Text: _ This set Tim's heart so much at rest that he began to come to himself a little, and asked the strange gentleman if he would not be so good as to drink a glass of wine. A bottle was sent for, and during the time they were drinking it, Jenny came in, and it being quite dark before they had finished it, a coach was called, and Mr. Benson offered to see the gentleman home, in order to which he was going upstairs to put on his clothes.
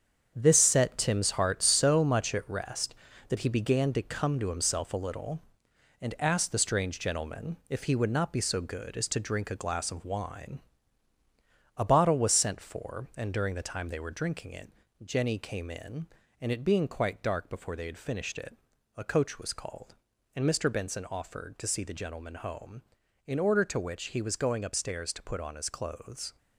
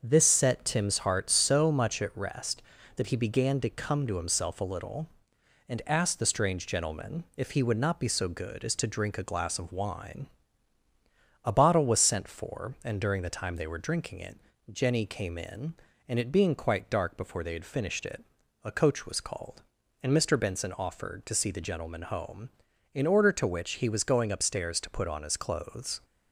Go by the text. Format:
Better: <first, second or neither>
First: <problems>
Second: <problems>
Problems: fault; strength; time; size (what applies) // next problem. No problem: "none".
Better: second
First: gets quieter; strong; throughout; 8 dB // starts louder than the rest; strong; until 1.3 s; 7.5 dB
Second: starts louder than the rest; until 1.0 s; 6.5 dB